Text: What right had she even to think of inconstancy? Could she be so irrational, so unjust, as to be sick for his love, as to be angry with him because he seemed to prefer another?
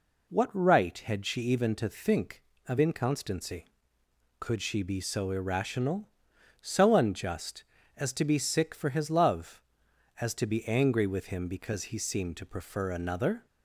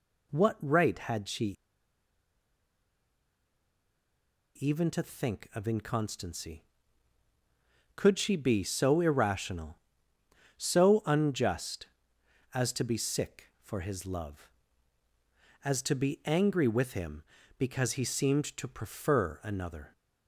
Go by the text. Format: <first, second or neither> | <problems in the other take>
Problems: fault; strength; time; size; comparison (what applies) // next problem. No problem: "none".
first | pauses between "she" and "even"; strong; at 1.5 s; 3.0 s long